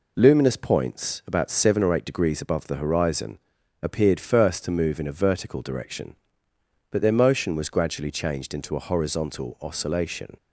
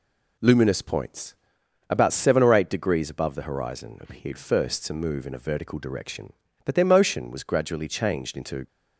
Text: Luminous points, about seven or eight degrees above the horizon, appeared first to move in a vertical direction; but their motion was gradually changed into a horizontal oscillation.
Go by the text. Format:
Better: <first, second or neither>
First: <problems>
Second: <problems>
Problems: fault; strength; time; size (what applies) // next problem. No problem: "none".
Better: first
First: none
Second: stops before "a horizontal oscillation"; at 8.6 s